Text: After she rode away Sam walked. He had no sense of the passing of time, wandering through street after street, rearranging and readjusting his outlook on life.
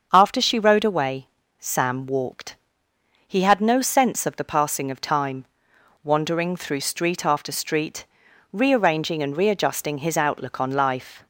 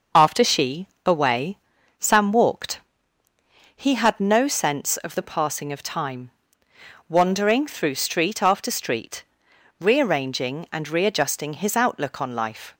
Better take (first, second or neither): first